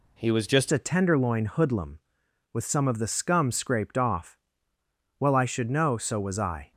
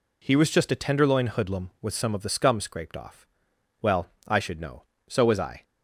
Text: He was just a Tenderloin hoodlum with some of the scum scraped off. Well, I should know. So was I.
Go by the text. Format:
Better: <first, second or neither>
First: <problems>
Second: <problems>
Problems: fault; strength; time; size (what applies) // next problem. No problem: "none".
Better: second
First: changes voice at "a"; from 0.7 s on; 6.0 s long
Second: none